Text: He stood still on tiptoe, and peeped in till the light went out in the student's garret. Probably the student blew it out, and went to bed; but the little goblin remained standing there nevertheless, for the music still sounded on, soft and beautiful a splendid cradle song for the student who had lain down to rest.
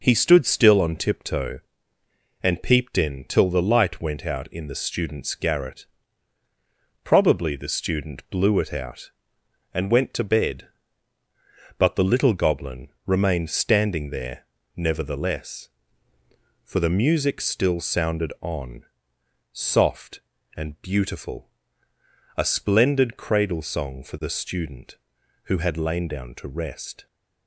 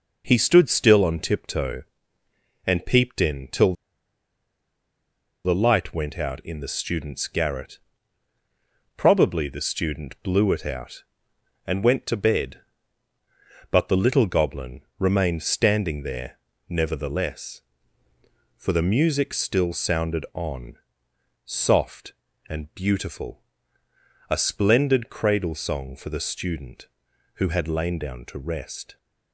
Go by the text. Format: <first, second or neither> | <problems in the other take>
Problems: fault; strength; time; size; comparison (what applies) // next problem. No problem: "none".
first | pauses between "till" and "the"; strong; at 3.7 s; 1.7 s long // pauses between "goblin" and "remained"; slight; at 14.8 s; 0.18 s long; slight in the first // pauses between "there" and "nevertheless"; slight; at 16.3 s; 0.30 s long; slight in the first // pauses between "beautiful" and "a"; noticeable; at 23.4 s; 0.88 s long; noticeable in the first